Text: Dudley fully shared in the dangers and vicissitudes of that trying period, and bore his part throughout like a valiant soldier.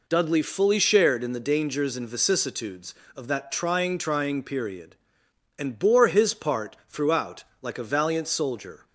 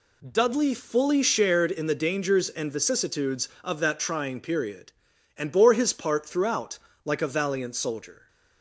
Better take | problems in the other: second | says "trying" twice; at 3.9 s // pauses between "throughout" and "like"; slight; at 7.4 s; 0.18 s long; slight in the second

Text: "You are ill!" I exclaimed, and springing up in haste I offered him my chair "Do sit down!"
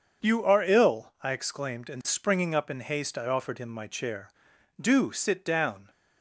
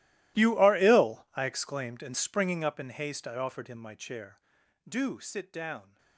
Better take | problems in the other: first | gets quieter; strong; throughout; 20.5 dB // starts louder than the rest; strong; until 1.4 s; 16 dB; also in the first

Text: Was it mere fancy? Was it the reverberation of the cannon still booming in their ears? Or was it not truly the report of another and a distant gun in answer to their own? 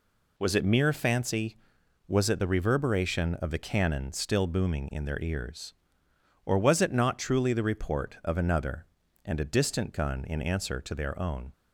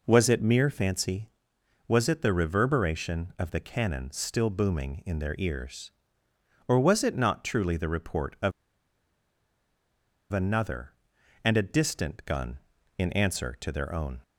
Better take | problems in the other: first | pauses between "of" and "another"; strong; at 8.5 s; 1.8 s long

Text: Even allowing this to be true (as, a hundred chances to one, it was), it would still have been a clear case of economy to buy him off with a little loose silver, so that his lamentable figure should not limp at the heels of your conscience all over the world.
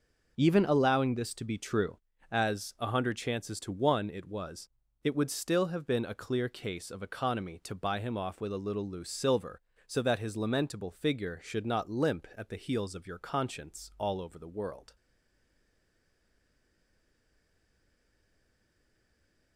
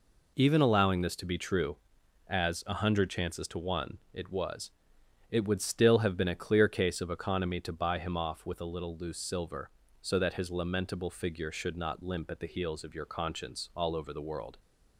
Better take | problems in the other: second | stays silent after the last word; strong; from 14.9 s on; 4.6 s long

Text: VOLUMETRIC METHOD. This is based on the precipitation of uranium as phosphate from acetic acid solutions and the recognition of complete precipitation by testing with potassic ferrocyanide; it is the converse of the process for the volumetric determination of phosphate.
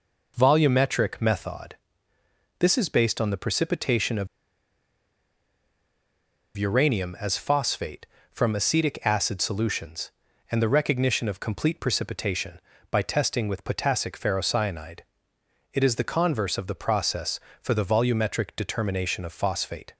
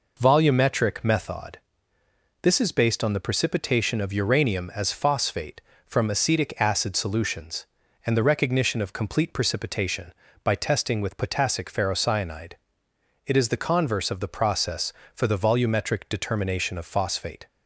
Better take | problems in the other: second | pauses between "of" and "uranium"; strong; at 4.2 s; 2.2 s long

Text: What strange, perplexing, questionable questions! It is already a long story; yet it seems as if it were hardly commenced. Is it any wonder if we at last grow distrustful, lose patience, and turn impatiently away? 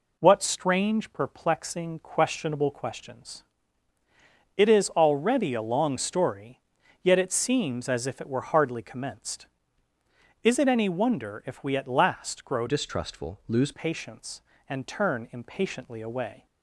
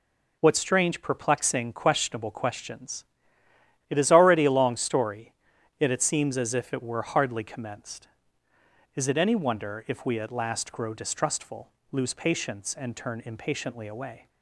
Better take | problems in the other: second | changes voice from "distrustful" to "lose"; from 12.6 to 13.7 s; 1.1 s long

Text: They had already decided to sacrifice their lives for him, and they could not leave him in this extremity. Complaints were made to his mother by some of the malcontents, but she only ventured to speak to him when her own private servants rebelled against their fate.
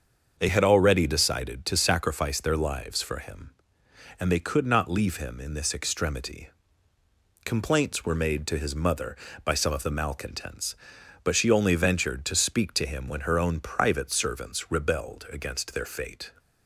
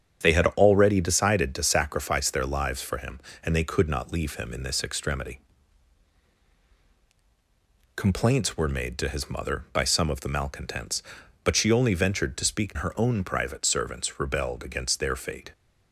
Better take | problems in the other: first | starts louder than the rest; strong; until 1.2 s; 8 dB; also in the first // skips "to him when"; at 12.7 s

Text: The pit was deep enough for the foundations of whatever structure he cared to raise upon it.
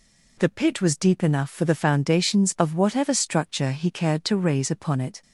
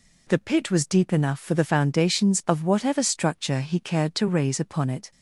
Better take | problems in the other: neither | none

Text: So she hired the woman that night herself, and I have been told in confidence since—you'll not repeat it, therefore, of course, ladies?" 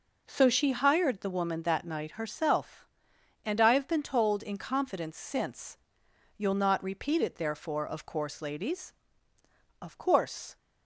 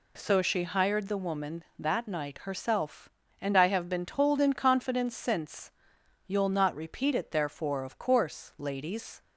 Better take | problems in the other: second | goes on to say "Of course"; noticeable; from 9.8 s on; 0.74 s long

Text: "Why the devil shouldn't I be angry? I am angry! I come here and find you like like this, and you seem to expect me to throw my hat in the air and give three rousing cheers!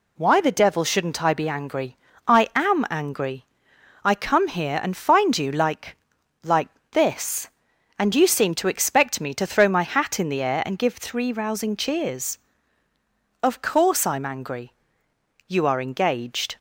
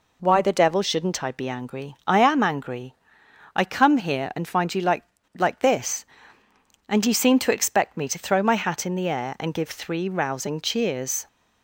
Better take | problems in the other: second | pauses between "like" and "like"; at 5.9 s; 0.44 s long; slight in the second // pauses between "like" and "this"; slight; at 6.6 s; 0.22 s long // goes on to say "Of course I'm angry You are engaged"; strong; from 13.4 s on; 3.1 s long

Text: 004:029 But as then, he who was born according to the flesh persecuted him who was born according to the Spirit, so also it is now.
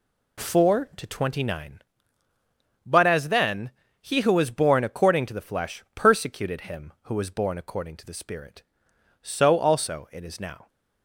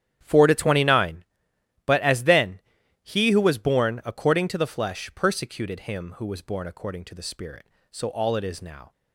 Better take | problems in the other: first | starts louder than the rest; strong; until 1.2 s; 10.5 dB // says "all" for "also"; at 8.0 s

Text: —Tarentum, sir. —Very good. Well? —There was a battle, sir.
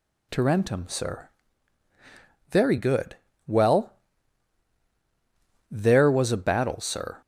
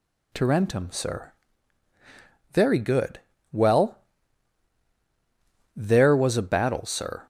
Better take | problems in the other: neither | none

